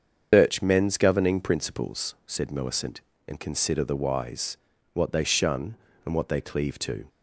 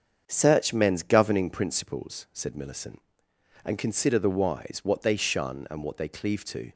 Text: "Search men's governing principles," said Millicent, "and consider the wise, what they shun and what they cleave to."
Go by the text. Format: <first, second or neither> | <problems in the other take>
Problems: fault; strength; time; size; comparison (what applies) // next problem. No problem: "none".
second | loses the start of "Search"; at 0.3 s; 170 ms // starts louder than the rest; until 1.3 s; 7 dB; also in the second